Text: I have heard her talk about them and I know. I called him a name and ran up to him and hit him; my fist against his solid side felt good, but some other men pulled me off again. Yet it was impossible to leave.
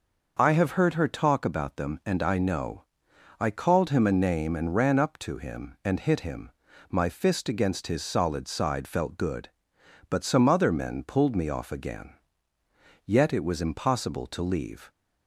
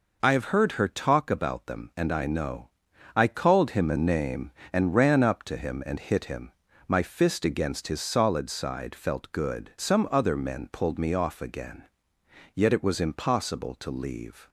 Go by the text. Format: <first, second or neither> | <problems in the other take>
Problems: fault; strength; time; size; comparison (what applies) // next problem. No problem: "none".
first | skips "but"; at 9.7 s